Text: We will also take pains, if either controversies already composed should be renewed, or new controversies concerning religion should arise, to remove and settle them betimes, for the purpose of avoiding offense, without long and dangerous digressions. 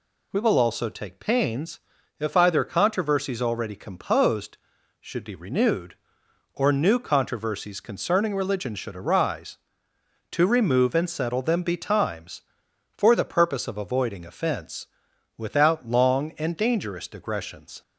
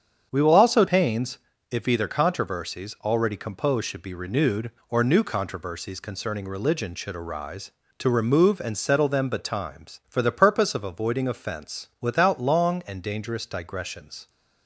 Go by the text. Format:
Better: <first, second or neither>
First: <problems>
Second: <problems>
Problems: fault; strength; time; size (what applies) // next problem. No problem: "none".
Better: first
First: none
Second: starts louder than the rest; strong; until 1.3 s; 7.5 dB // skips "take"; at 0.8 s